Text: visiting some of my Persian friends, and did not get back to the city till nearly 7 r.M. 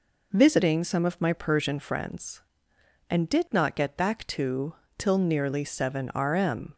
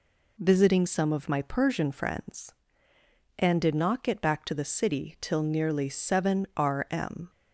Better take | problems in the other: second | skips "the city"; at 4.8 s

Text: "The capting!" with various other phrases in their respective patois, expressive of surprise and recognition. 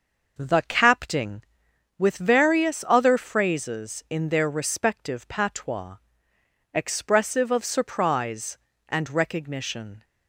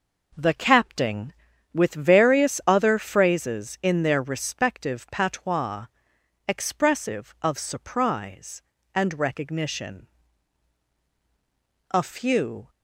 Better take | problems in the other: first | goes on to say "A few"; noticeable; from 11.9 s on; 0.78 s long

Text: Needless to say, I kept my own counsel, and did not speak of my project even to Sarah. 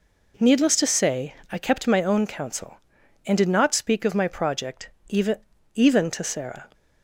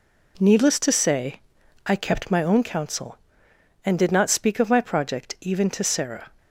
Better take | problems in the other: second | pauses between "project" and "even"; slight; at 4.8 s; 0.18 s long // says "even" twice; at 5.7 s

